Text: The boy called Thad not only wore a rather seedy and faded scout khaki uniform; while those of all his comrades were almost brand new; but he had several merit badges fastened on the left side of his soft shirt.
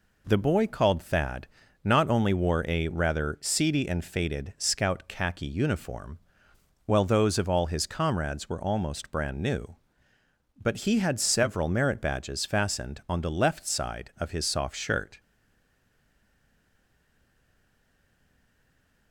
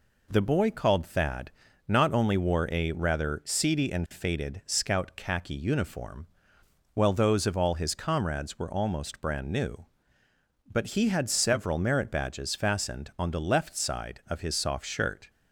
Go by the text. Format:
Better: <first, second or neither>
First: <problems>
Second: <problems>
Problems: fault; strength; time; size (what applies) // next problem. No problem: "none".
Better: second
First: pauses between "Thad" and "not"; at 1.4 s; 0.38 s long // stays silent after the last word; strong; from 15.1 s on; 4.0 s long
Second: pauses between "Thad" and "not"; at 1.4 s; 0.38 s long